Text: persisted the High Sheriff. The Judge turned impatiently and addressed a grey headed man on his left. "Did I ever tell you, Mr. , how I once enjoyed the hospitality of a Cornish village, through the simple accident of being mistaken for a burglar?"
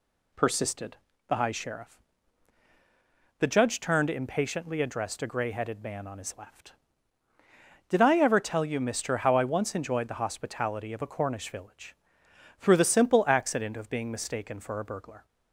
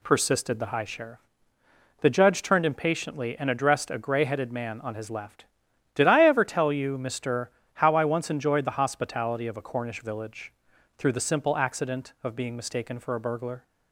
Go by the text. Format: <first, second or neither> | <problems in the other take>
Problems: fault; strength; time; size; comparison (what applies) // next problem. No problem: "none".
second | pauses between "persisted" and "the"; slight; at 0.9 s; 0.32 s long // skips "and"; at 4.8 s